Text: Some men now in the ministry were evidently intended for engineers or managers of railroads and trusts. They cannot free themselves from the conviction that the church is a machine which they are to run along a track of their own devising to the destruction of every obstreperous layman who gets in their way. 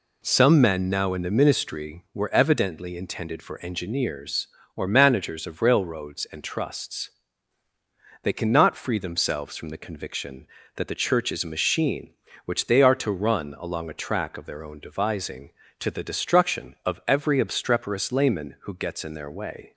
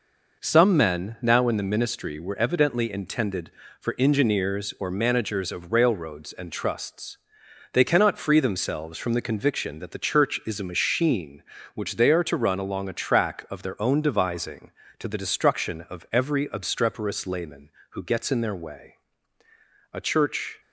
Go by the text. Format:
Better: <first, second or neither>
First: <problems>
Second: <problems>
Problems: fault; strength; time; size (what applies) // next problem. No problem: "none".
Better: first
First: none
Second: goes on to say "A church"; noticeable; from 19.9 s on; 0.68 s long